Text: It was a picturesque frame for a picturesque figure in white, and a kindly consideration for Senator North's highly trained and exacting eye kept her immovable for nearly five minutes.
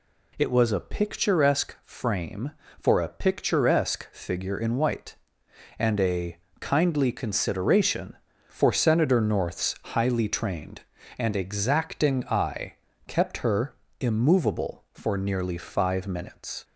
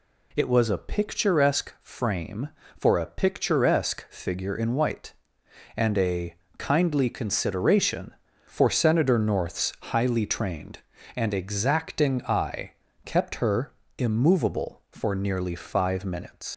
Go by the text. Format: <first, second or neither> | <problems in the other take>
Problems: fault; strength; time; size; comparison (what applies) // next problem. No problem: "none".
first | pauses between "a" and "kindly"; slight; at 6.3 s; 0.22 s long; slight in the first // pauses between "eye" and "kept"; slight; at 12.7 s; 0.32 s long; slight in the first // pauses between "her" and "immovable"; slight; at 13.7 s; 0.26 s long; slight in the first // leaves "minutes" unfinished; at 16.5 s; 70 ms